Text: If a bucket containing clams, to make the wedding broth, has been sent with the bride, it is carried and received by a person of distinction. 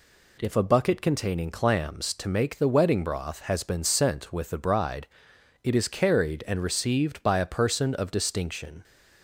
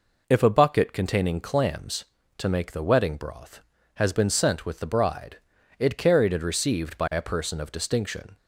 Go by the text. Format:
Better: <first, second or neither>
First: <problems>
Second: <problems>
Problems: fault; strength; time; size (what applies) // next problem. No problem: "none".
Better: first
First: none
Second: skips "is"; at 5.9 s